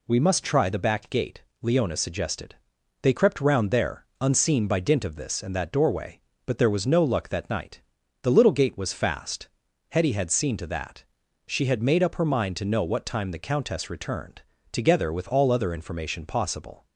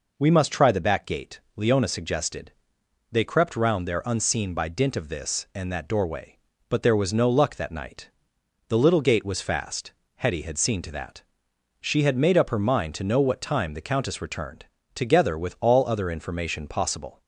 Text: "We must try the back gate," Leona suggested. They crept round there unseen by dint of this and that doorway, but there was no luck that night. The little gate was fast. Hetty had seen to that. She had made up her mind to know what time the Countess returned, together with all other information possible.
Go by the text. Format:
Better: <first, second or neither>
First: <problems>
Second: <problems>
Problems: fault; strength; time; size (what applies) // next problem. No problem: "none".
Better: neither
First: none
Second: none